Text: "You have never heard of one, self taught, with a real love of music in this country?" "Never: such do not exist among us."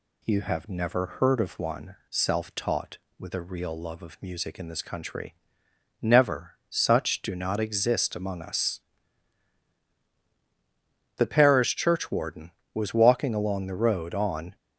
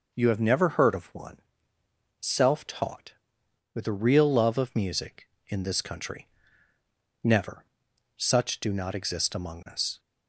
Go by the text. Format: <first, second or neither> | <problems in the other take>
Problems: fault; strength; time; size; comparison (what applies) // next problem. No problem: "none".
second | goes on to say "The parish churchwarden was walking along the road on"; strong; from 11.1 s on; 3.3 s long